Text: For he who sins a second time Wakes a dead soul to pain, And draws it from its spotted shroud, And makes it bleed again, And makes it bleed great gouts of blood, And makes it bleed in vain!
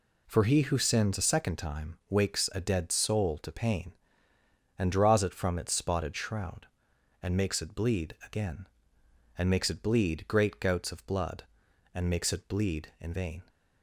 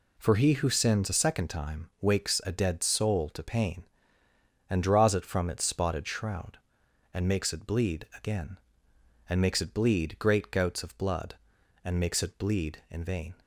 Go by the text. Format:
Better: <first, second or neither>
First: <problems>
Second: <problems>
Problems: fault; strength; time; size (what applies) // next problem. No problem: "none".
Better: neither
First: none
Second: none